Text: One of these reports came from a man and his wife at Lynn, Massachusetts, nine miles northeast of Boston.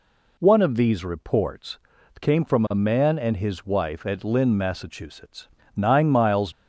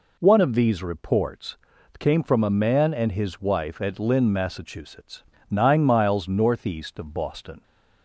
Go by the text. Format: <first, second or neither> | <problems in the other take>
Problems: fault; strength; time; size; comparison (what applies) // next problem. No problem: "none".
second | pauses between "reports" and "came"; at 1.7 s; 0.40 s long; also in the second // stops before "northeast of Boston"; at 6.5 s